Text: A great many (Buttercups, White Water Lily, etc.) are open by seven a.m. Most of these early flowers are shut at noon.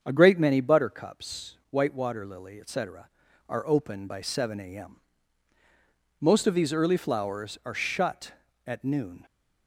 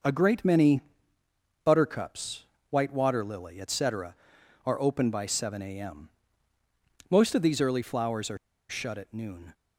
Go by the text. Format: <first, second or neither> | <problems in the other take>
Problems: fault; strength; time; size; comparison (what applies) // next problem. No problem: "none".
first | starts louder than the rest; noticeable; until 1.8 s; 6 dB; strong in the first // pauses between "are" and "shut"; slight; at 8.3 s; 0.31 s long